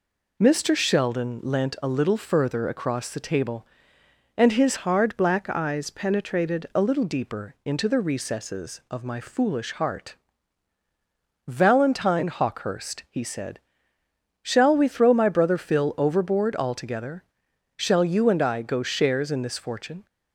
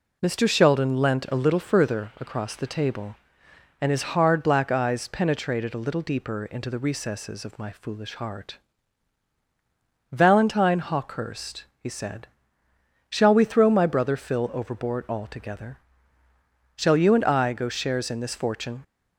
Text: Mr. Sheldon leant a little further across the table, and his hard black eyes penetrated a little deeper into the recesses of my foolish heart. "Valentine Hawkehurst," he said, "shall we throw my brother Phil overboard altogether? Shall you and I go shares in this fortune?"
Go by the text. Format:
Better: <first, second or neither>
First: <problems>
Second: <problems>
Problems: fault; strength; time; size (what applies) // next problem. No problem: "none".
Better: second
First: changes voice from "hard" to "penetrated"; from 4.7 to 6.6 s; 1.9 s long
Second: none